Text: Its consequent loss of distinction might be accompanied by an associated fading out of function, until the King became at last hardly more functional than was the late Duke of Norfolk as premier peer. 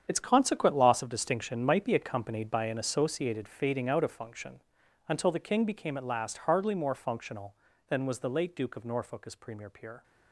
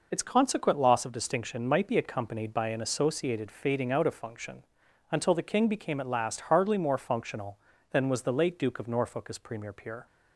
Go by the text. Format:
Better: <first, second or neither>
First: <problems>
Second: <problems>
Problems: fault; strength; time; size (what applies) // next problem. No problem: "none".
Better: second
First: gets quieter; strong; throughout; 13 dB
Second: none